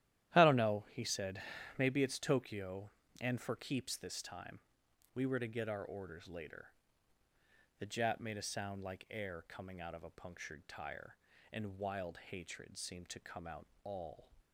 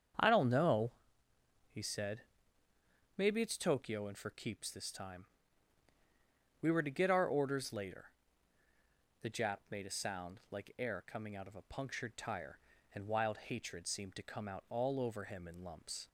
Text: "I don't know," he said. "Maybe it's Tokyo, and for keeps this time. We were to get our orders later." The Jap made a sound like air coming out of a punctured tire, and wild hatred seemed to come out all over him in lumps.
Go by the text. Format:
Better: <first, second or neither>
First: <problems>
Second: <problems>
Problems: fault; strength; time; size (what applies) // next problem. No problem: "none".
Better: second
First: starts louder than the rest; strong; until 1.3 s; 12.5 dB // pauses between "out" and "all"; slight; at 13.6 s; 0.16 s long // stops before "over him in lumps"; at 14.3 s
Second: starts louder than the rest; strong; until 1.9 s; 7.5 dB